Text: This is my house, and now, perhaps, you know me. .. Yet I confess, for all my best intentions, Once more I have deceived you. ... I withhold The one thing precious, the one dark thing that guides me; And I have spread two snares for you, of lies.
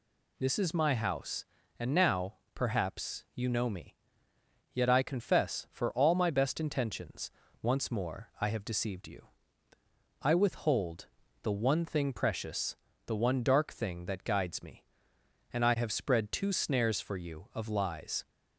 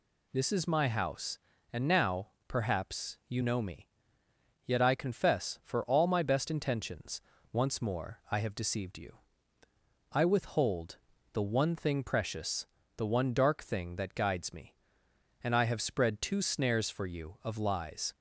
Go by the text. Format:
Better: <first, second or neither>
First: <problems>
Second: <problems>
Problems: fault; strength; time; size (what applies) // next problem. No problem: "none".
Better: neither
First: pauses between "withhold" and "The"; slight; at 11.0 s; 0.36 s long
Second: pauses between "withhold" and "The"; slight; at 10.9 s; 0.36 s long